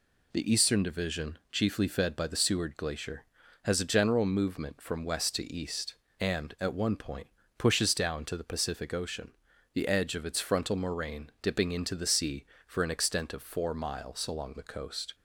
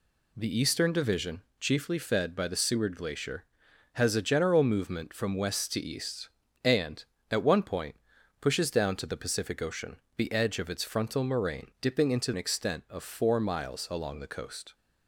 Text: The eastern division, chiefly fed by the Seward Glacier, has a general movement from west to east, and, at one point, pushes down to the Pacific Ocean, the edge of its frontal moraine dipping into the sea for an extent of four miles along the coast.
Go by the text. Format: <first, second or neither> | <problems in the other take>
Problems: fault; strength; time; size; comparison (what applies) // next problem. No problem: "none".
first | skips "the sea for"; at 12.3 s